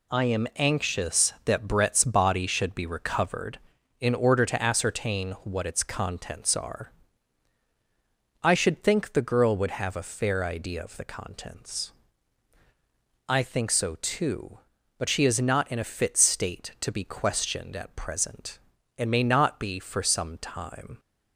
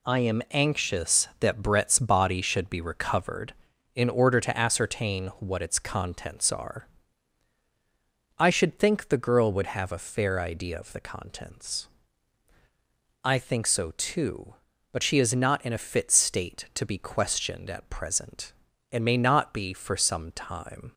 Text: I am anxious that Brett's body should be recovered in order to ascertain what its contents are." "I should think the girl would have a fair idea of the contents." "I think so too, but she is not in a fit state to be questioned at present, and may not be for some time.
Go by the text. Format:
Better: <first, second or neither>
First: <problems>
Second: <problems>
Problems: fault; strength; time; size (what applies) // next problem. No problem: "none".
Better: neither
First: none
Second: none